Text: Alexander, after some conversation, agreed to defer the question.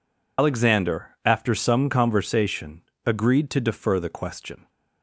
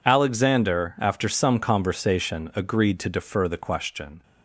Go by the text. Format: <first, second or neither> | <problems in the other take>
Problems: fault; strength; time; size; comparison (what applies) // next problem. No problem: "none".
second | loses the start of "Alexander"; at 0.3 s; 110 ms